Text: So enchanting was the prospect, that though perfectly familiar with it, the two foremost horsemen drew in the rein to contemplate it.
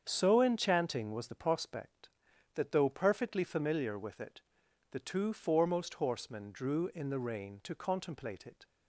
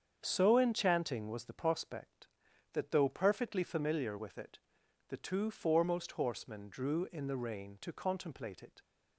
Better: neither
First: starts louder than the rest; strong; until 1.0 s; 7.5 dB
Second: starts louder than the rest; strong; until 1.2 s; 7.5 dB

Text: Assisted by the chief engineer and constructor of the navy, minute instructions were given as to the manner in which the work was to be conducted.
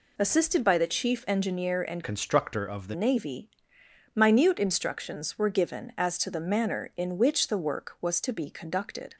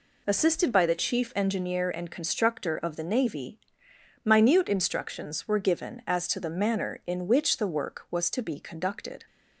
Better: second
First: changes voice from "constructor" to "the"; from 2.0 to 2.9 s; 0.9 s long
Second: none

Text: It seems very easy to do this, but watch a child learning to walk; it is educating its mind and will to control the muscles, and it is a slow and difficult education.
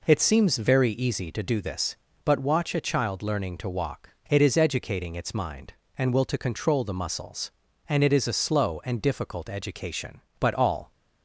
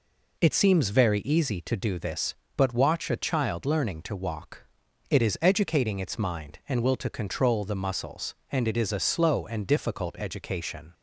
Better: second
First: goes on to say "But all"; from 10.4 s on; 0.52 s long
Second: none

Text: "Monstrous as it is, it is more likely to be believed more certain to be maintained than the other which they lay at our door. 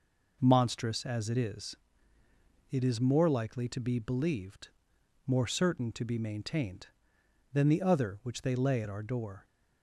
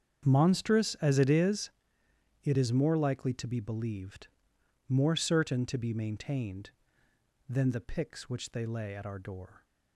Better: first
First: pauses between "believed" and "more"; noticeable; at 4.6 s; 0.60 s long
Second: starts louder than the rest; strong; until 1.3 s; 7.5 dB // pauses between "believed" and "more"; noticeable; at 4.2 s; 0.58 s long // says "picks" for "other"; at 7.8 s

